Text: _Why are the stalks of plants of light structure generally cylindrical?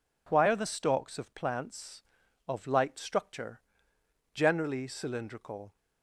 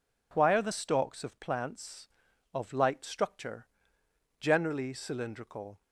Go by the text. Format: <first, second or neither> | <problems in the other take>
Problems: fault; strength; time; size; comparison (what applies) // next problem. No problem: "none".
neither | pauses between "structure" and "generally"; noticeable; the same in both